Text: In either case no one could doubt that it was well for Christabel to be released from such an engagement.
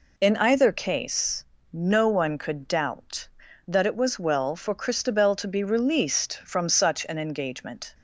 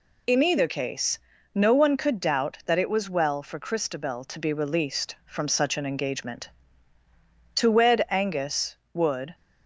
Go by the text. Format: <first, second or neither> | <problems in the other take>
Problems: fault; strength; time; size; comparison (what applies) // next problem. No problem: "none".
first | pauses between "case" and "no"; at 1.1 s; 0.38 s long; slight in the first // goes on to say "To wed Angus would"; strong; from 7.5 s on; 1.8 s long